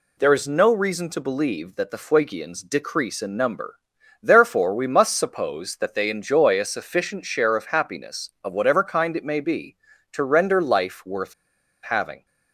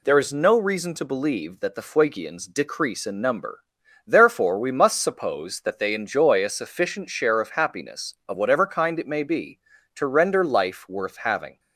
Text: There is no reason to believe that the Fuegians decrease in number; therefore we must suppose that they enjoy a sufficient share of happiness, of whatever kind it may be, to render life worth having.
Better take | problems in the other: second | pauses between "worth" and "having"; noticeable; at 11.3 s; 0.49 s long

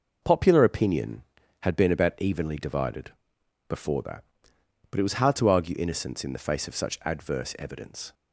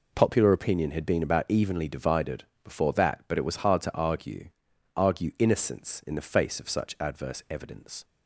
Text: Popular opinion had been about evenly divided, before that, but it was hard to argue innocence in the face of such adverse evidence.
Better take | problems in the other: first | says "argue" twice; at 4.9 s

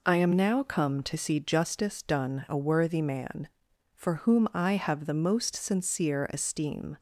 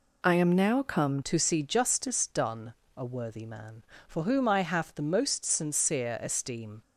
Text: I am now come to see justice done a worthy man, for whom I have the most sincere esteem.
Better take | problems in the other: first | changes voice at "to"; from 1.2 s on; 5.6 s long // pauses between "done" and "a"; slight; at 2.7 s; 0.22 s long

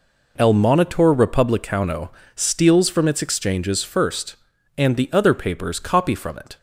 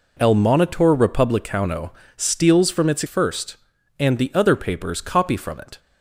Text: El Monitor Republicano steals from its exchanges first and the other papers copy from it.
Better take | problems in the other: first | pauses between "Republicano" and "steals"; slight; at 1.9 s; 0.24 s long; slight in the first // skips "exchanges"; at 3.0 s

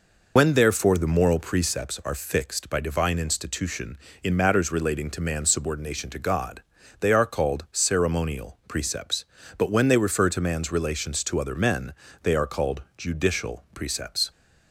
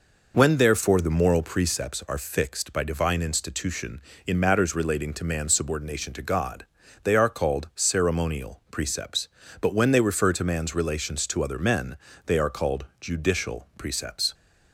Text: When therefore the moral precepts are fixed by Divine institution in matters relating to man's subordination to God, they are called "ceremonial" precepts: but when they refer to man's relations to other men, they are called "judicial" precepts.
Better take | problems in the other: second | loses the start of "When"; at 0.3 s; 45 ms // pauses between "called" and "judicial"; slight; at 12.8 s; 0.16 s long; slight in the second

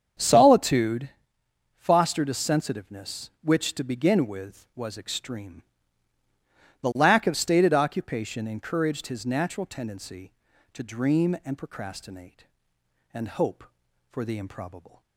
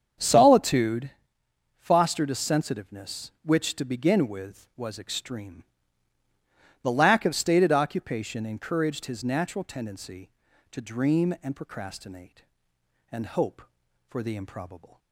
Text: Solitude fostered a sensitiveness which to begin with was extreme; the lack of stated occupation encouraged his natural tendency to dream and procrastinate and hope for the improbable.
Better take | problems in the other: neither | starts louder than the rest; strong; the same in both // pauses between "Solitude" and "fostered"; noticeable; the same in both

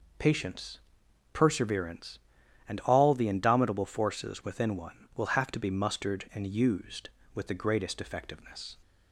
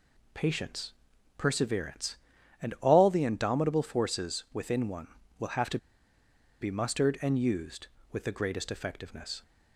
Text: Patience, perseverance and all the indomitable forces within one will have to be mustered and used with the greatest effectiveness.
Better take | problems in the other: first | pauses between "to" and "be"; noticeable; at 5.7 s; 0.82 s long

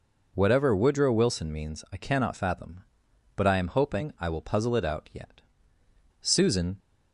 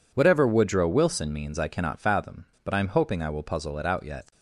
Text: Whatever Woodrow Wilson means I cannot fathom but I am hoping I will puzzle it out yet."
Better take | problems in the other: second | goes on to say "Susan"; from 6.2 s on; 0.58 s long

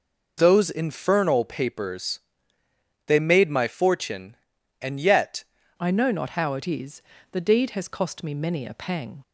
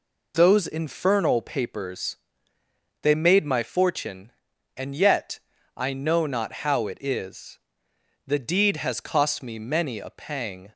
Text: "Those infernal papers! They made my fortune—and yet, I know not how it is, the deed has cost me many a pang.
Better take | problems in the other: second | changes voice at "I"; from 5.7 s on; 3.5 s long

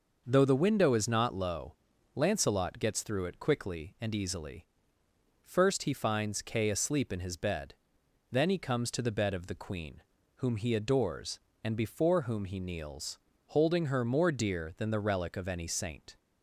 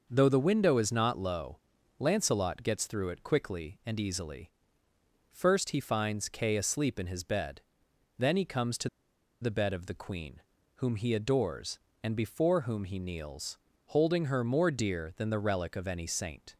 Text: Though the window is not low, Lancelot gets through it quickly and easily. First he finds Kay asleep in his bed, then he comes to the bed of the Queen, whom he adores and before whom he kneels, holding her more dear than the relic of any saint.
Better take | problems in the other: first | pauses between "to" and "the"; noticeable; at 8.8 s; 0.53 s long

